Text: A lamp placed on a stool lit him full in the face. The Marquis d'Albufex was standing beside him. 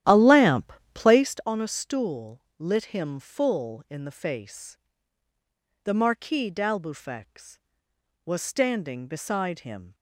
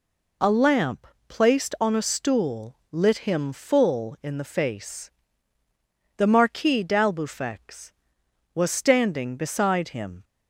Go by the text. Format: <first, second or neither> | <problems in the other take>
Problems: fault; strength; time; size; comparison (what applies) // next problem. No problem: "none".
second | starts louder than the rest; strong; until 1.4 s; 12 dB // pauses between "lamp" and "placed"; slight; at 0.7 s; 0.22 s long; slight in the second // pauses between "stool" and "lit"; slight; at 2.4 s; 0.16 s long